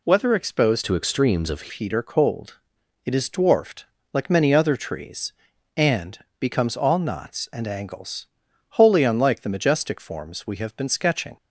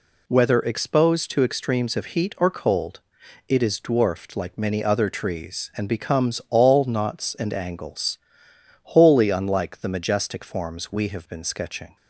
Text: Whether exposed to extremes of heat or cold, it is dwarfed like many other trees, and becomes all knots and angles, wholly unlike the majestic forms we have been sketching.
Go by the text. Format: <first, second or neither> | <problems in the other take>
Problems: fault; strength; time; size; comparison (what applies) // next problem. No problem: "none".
second | changes voice from "to" to "of"; from 0.8 to 1.6 s; 0.8 s long // pauses between "dwarfed" and "like"; slight; at 3.8 s; 0.26 s long // pauses between "and" and "becomes"; slight; at 6.1 s; 0.20 s long